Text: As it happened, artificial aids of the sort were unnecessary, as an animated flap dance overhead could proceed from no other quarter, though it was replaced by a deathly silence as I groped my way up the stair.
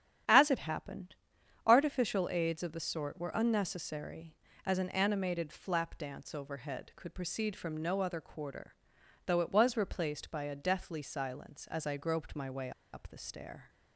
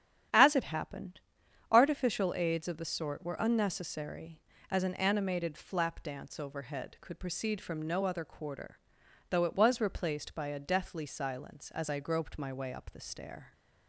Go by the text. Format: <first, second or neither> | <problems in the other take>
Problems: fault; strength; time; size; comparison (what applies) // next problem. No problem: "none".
second | starts louder than the rest; strong; until 1.7 s; 9.5 dB; strong in the second // pauses between "way" and "up"; slight; at 12.7 s; 0.22 s long